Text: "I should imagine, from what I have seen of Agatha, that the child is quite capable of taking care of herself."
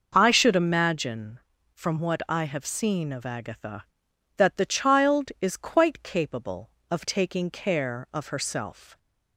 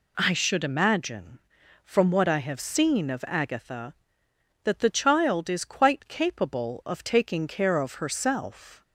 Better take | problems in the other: neither | none

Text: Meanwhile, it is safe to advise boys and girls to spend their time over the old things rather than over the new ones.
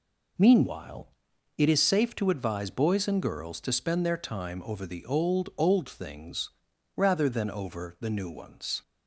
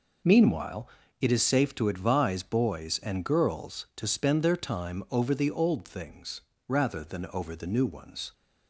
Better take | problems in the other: second | says "old" twice; at 5.5 s // pauses between "things" and "rather"; noticeable; at 6.4 s; 0.48 s long; slight in the second

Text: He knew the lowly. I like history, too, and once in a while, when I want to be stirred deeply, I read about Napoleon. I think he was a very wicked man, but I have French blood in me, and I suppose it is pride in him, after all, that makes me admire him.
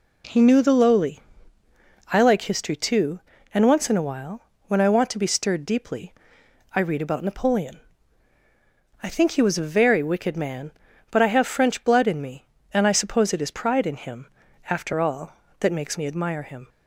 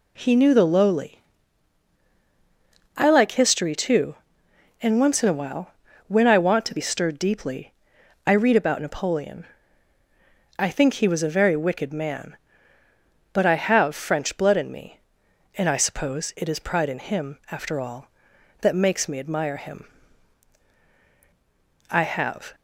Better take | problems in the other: first | goes on to say "I have"; noticeable; from 21.9 s on; 0.64 s long

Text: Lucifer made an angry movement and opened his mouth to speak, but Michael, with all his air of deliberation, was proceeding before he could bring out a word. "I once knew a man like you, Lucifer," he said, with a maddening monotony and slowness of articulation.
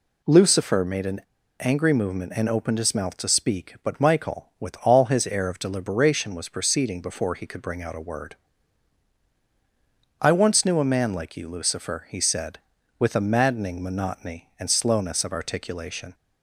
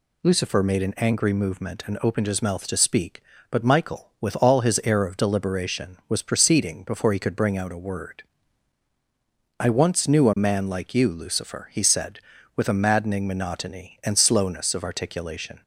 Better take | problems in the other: second | pauses between "an" and "angry"; at 1.2 s; 0.40 s long

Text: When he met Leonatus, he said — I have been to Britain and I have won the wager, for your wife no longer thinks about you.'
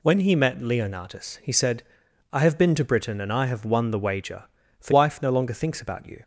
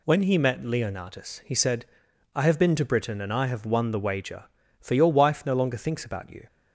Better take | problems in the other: second | skips "your"; at 4.9 s

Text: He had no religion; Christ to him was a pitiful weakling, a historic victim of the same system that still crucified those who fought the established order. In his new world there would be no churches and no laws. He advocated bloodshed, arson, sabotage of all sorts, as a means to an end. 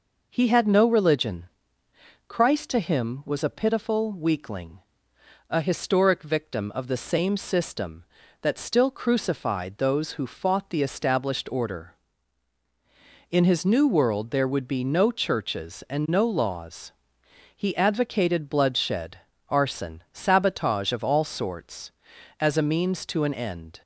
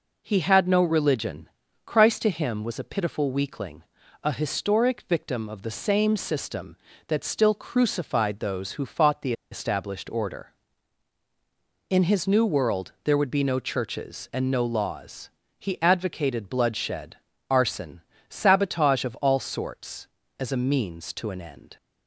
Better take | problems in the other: first | pauses between "the" and "established"; slight; at 9.3 s; 0.19 s long

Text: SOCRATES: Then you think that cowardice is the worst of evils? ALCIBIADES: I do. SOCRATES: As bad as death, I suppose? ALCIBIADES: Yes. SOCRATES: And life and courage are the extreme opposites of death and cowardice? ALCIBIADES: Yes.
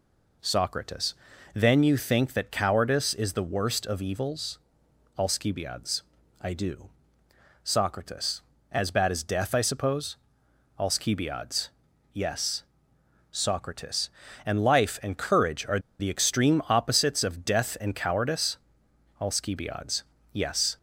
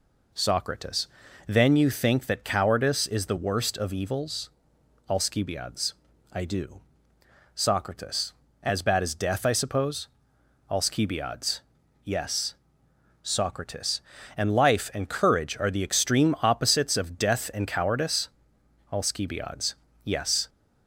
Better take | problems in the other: second | pauses between "are" and "the"; slight; at 15.7 s; 0.20 s long

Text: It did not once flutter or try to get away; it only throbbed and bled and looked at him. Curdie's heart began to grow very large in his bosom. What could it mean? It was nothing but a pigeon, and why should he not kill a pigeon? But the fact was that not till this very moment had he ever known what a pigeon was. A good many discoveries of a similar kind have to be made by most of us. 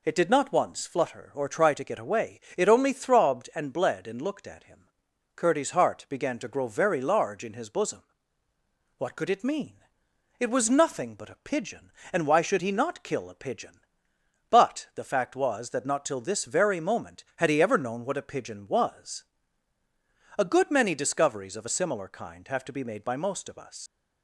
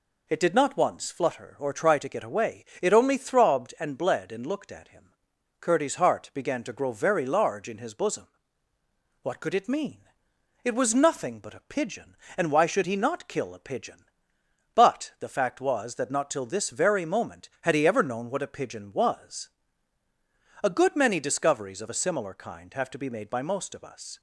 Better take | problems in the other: second | leaves "us" unfinished; at 23.8 s; 80 ms

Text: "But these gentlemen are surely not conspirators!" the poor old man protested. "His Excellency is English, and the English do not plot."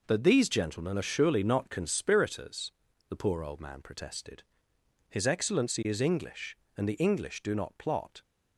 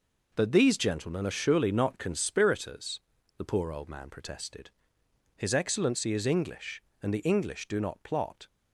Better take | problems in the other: neither | none

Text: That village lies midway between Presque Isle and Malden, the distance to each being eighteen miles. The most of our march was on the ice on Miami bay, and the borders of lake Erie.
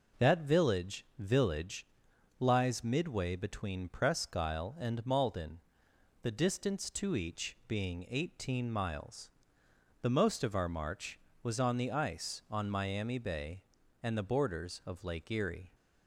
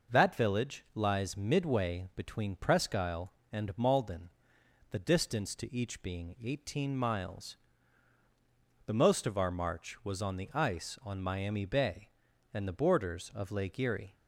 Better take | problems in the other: second | says "village" twice; at 1.1 s

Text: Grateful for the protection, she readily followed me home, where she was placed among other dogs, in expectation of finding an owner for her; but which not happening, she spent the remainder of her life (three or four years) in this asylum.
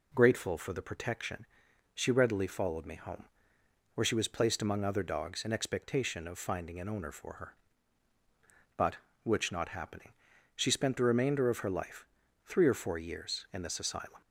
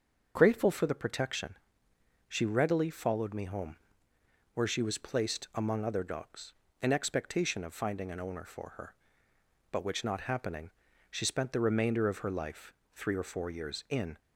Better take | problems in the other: first | starts louder than the rest; until 1.3 s; 6.5 dB // stops before "this asylum"; at 14.1 s

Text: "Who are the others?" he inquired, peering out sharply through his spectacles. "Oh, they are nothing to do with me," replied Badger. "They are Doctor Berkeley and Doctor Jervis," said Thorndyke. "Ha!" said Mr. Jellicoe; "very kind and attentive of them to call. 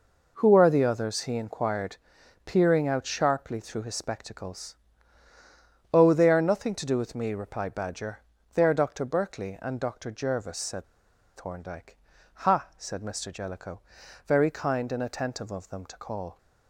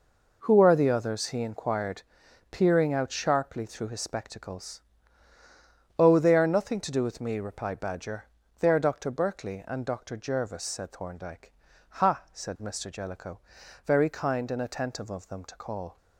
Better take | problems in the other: second | pauses between "said" and "Thorndyke"; noticeable; at 10.8 s; 0.52 s long

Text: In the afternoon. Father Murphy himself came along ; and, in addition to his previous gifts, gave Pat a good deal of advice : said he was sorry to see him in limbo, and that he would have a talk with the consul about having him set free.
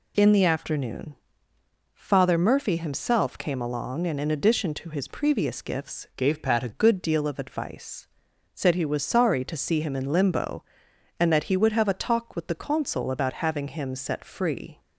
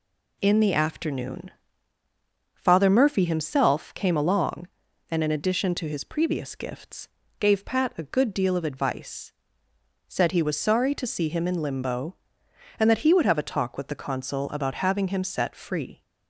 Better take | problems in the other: second | changes voice from "gave" to "a"; from 6.1 to 6.6 s; 0.5 s long

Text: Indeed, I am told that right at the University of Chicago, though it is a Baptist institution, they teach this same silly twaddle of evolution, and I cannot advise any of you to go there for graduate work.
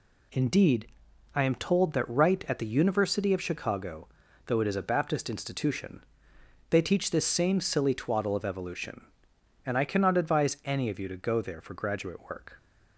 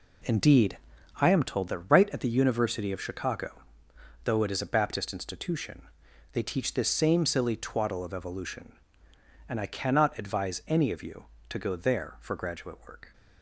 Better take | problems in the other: first | starts louder than the rest; slight; until 1.4 s; 3.5 dB

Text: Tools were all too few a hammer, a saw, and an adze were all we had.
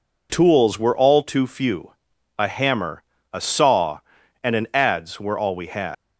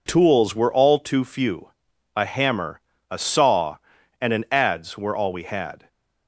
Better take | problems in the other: second | pauses between "few" and "a"; at 1.9 s; 0.44 s long; also in the second // leaves "had" unfinished; at 5.9 s; 165 ms

